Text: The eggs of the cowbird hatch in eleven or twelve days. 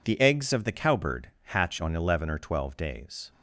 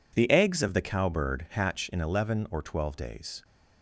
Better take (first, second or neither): second